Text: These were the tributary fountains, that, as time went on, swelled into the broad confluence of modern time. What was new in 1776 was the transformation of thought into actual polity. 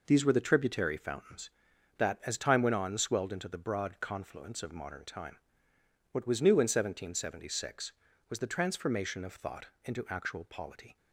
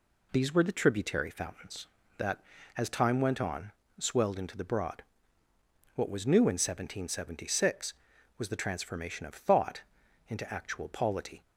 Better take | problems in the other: first | skips "confluence of modern time"; at 5.4 s // pauses between "thought" and "into"; noticeable; at 9.8 s; 0.48 s long; slight in the first

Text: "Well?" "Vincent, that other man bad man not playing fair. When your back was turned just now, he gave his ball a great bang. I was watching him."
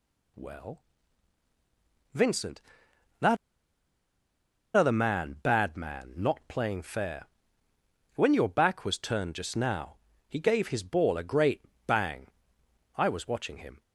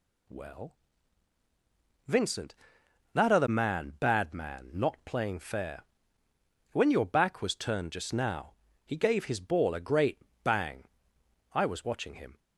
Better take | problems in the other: second | pauses between "that" and "other"; strong; at 3.3 s; 1.4 s long // pauses between "great" and "bang"; slight; at 11.6 s; 0.24 s long; slight in the second

